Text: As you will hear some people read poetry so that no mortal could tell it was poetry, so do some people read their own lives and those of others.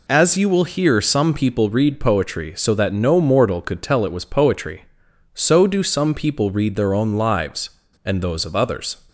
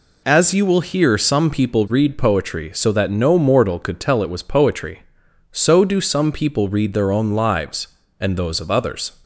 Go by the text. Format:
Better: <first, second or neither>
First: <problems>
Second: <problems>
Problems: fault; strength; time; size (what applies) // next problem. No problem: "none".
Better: neither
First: none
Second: none